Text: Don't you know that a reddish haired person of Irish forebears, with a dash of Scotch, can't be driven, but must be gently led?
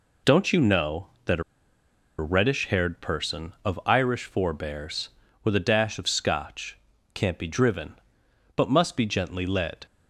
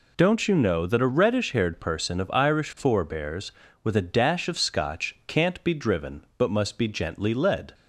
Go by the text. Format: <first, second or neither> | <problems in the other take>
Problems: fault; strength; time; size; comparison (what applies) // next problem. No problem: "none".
second | pauses between "a" and "reddish"; noticeable; at 1.4 s; 0.76 s long